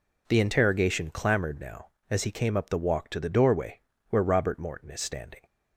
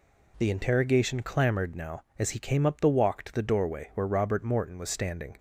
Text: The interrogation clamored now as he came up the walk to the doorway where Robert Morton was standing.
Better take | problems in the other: second | pauses between "doorway" and "where"; slight; at 3.8 s; 0.28 s long // says "is" for "was"; at 4.8 s

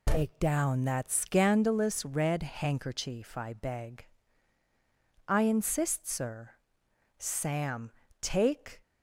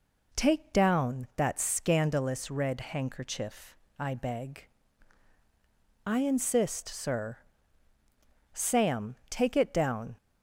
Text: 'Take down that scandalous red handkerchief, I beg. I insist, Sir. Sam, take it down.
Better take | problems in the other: second | stops before "it down"; at 8.8 s

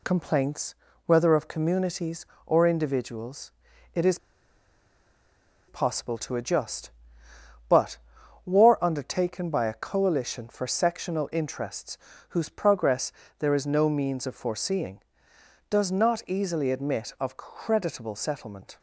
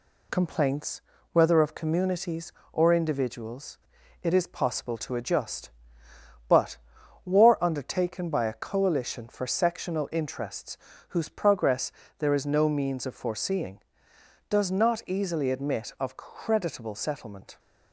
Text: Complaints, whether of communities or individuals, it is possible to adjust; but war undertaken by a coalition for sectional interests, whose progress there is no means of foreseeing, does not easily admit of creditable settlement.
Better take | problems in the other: second | pauses between "is" and "possible"; strong; at 4.1 s; 1.5 s long // pauses between "but" and "war"; noticeable; at 7.9 s; 0.48 s long; noticeable in the second // pauses between "progress" and "there"; slight; at 13.1 s; 0.26 s long; slight in the second

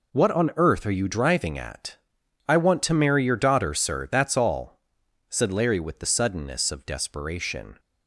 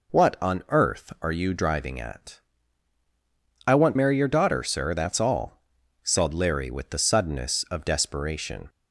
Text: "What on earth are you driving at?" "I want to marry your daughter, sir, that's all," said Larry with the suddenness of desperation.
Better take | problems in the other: first | skips "to"; at 3.9 s

